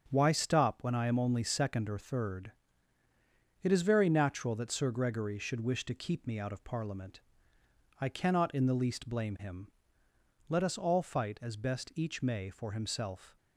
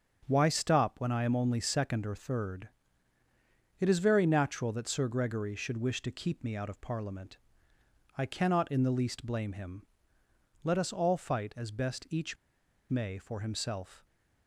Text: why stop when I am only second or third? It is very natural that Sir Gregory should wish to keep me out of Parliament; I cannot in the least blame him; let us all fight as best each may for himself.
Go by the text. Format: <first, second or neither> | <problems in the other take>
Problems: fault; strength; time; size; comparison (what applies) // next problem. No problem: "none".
first | starts louder than the rest; until 1.3 s; 7 dB; also in the first // pauses between "each" and "may"; noticeable; at 12.3 s; 0.55 s long